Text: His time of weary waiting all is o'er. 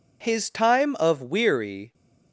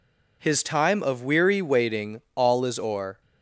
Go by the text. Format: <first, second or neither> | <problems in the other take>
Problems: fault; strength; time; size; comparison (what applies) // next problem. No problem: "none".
second | stops before "waiting all is o'er"; at 1.9 s